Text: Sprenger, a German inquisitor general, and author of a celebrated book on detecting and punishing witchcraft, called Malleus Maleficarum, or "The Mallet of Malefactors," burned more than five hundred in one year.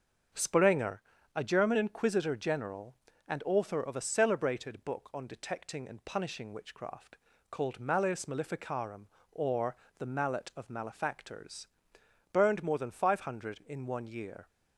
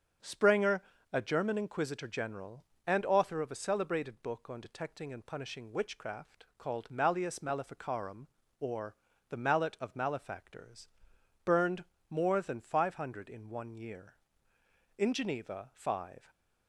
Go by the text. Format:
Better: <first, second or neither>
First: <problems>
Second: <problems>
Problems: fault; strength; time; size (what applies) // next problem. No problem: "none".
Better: first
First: starts louder than the rest; until 1.6 s; 6.5 dB // pauses between "or" and "The"; slight; at 9.7 s; 0.22 s long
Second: starts louder than the rest; strong; until 1.4 s; 7.5 dB // pauses between "or" and "The"; slight; at 8.9 s; 0.34 s long // pauses between "burned" and "more"; slight; at 11.8 s; 0.26 s long // goes on to say "In Geneva five"; from 14.9 s on; 1.3 s long